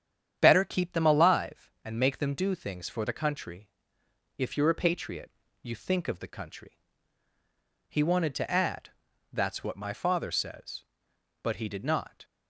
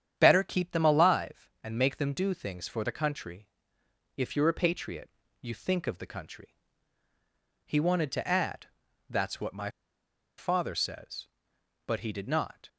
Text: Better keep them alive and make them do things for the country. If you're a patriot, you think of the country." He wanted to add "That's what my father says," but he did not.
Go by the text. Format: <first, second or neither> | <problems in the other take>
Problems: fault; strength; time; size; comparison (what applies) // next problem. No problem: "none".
first | starts louder than the rest; strong; until 1.1 s; 9 dB; strong in the first // pauses between "add" and "That's"; at 8.6 s; 0.42 s long; also in the first // pauses between "my" and "father"; noticeable; at 9.6 s; 0.68 s long